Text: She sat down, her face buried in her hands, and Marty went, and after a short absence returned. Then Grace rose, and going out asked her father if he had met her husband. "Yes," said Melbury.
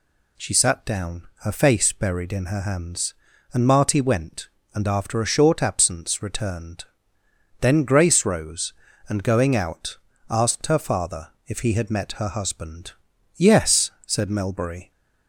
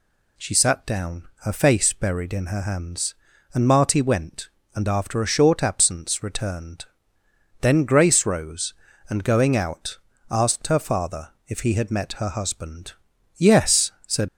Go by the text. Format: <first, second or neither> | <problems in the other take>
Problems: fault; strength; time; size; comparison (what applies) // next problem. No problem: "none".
first | pauses between "out" and "asked"; slight; at 9.9 s; 0.32 s long; slight in the first // pauses between "father" and "if"; slight; at 11.2 s; 0.18 s long; slight in the first // stops before "Melbury"; at 14.2 s